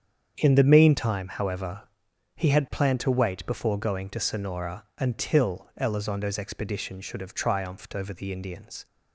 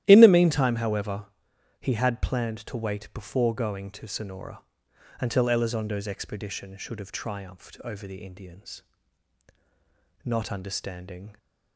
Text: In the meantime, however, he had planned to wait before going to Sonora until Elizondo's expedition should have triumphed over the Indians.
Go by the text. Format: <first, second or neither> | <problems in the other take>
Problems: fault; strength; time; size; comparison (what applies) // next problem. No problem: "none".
first | starts louder than the rest; strong; until 1.0 s; 13 dB; strong in the first // pauses between "Sonora" and "until"; noticeable; at 4.6 s; 0.60 s long // goes on to say "Not understanding"; noticeable; from 10.2 s on; 1.1 s long